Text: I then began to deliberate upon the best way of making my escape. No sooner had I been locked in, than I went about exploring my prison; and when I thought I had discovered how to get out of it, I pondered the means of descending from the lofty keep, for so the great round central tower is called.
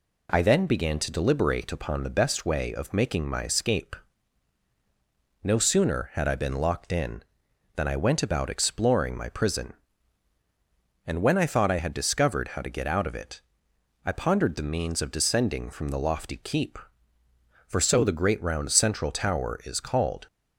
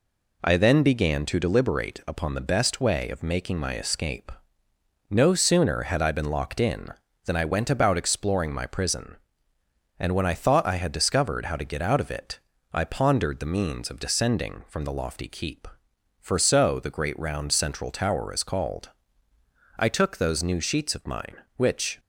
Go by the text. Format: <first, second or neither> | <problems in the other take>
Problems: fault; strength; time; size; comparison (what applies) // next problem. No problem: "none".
first | goes on to say "I took those new sheets of mine which"; strong; from 19.7 s on; 2.2 s long